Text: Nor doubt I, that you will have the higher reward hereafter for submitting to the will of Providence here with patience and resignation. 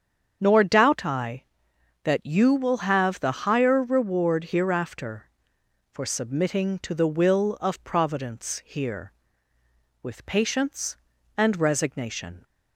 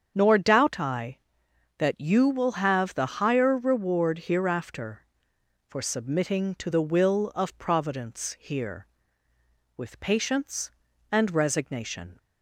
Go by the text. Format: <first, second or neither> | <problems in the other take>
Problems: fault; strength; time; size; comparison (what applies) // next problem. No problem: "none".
neither | starts louder than the rest; strong; the same in both